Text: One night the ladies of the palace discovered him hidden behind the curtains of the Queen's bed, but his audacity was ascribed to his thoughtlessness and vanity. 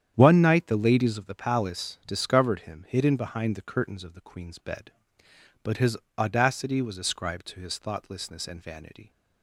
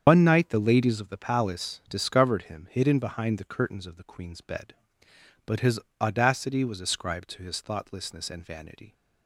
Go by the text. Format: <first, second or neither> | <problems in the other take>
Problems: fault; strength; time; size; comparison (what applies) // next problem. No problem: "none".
first | loses the start of "One"; at 0.0 s; 85 ms // starts louder than the rest; strong; until 1.0 s; 8 dB; strong in the first // pauses between "his" and "audacity"; slight; at 5.7 s; 0.22 s long; slight in the first